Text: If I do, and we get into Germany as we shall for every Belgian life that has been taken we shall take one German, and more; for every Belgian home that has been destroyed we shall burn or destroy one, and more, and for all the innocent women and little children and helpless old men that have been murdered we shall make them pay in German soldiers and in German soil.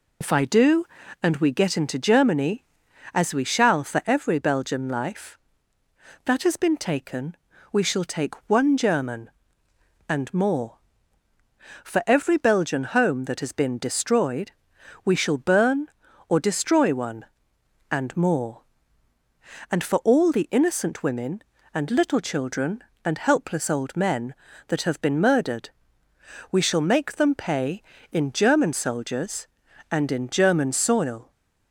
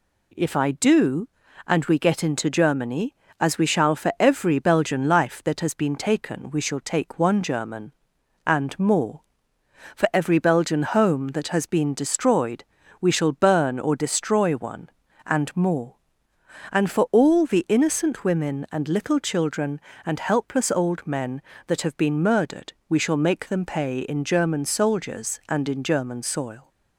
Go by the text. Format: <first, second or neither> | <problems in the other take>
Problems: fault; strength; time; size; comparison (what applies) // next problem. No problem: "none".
second | loses the start of "If"; at 0.2 s; 45 ms // pauses between "taken" and "we"; slight; at 7.3 s; 0.36 s long // pauses between "destroyed" and "we"; noticeable; at 14.5 s; 0.52 s long; slight in the second // pauses between "murdered" and "we"; noticeable; at 25.6 s; 0.82 s long; slight in the second